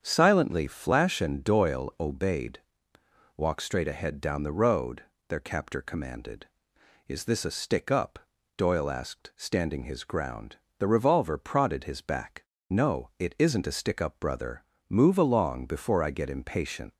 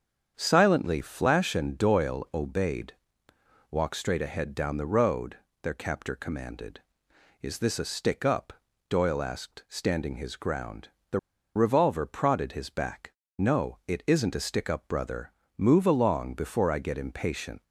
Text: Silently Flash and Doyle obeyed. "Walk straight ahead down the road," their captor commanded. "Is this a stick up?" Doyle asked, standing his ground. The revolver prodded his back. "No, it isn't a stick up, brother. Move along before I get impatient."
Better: first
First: starts louder than the rest; strong; until 1.0 s; 7.5 dB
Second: starts louder than the rest; strong; until 1.3 s; 8 dB // pauses between "The" and "revolver"; at 11.1 s; 0.37 s long

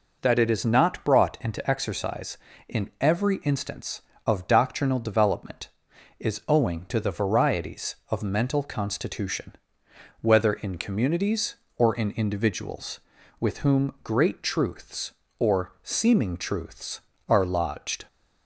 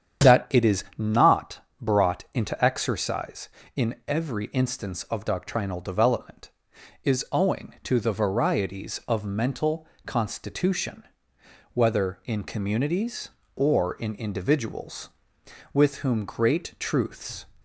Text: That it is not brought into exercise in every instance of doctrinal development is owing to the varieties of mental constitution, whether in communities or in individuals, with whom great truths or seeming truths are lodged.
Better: first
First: none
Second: starts louder than the rest; strong; until 1.3 s; 8.5 dB // pauses between "not" and "brought"; slight; at 1.5 s; 0.22 s long // pauses between "mental" and "constitution"; slight; at 9.8 s; 0.22 s long // stops before "or seeming truths are lodged"; at 17.5 s

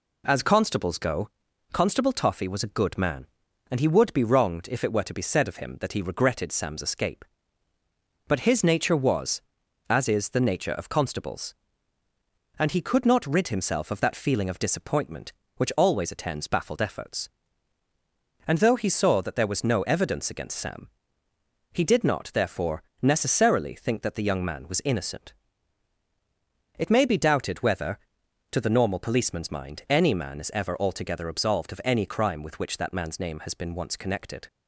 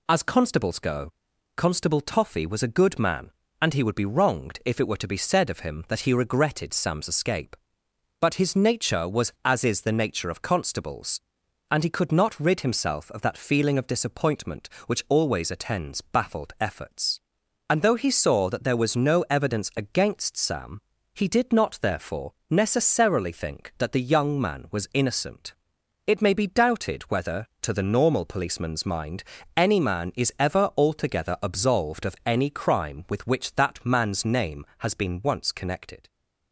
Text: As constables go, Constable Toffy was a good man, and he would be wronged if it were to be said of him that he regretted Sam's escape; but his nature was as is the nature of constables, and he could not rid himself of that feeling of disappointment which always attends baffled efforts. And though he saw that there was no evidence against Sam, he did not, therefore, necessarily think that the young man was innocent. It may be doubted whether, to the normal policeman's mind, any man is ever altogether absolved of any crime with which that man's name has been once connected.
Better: neither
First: none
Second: none

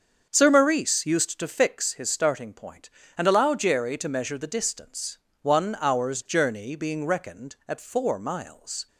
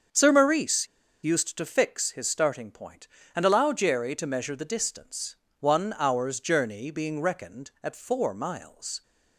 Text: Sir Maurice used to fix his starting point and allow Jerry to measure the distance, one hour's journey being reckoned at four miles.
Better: first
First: starts louder than the rest; until 1.3 s; 7 dB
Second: starts louder than the rest; until 1.4 s; 7 dB // pauses between "Maurice" and "used"; at 0.8 s; 0.36 s long

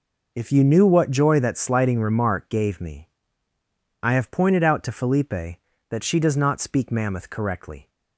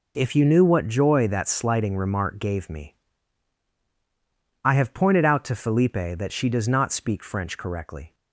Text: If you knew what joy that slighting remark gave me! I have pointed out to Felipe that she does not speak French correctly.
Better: second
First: says "Mammoth" for "French"; at 6.9 s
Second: none

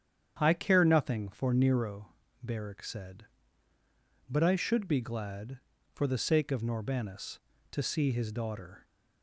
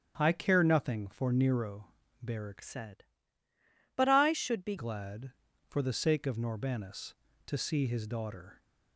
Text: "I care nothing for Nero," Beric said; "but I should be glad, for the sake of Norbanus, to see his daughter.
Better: first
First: starts louder than the rest; strong; until 1.4 s; 8.5 dB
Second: starts louder than the rest; strong; until 1.1 s; 8.5 dB // changes voice from "said" to "be"; from 2.6 to 4.7 s; 2.1 s long

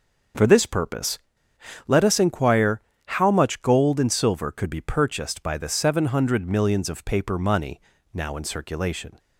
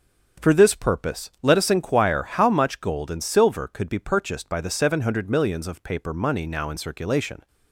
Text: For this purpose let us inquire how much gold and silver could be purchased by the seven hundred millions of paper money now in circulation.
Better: second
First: starts louder than the rest; until 2.0 s; 6.5 dB // pauses between "purpose" and "let"; noticeable; at 1.1 s; 0.70 s long // pauses between "inquire" and "how"; slight; at 2.8 s; 0.26 s long // pauses between "money" and "now"; slight; at 7.8 s; 0.32 s long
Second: starts louder than the rest; strong; until 1.5 s; 7 dB

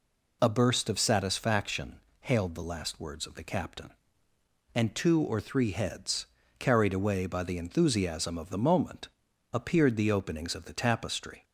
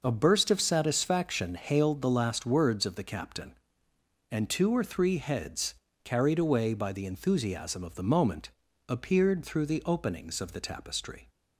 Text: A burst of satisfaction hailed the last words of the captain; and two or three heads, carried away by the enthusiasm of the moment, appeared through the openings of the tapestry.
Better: second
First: pauses between "satisfaction" and "hailed"; slight; at 1.9 s; 0.26 s long // skips "through"; at 9.9 s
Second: none

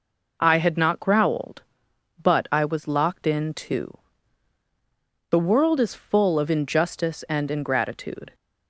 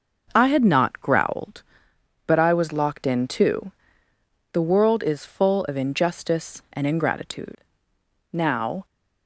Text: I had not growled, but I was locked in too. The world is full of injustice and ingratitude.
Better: first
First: none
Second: starts louder than the rest; noticeable; until 1.3 s; 6 dB // goes on to say "Now"; from 8.3 s on; 0.54 s long

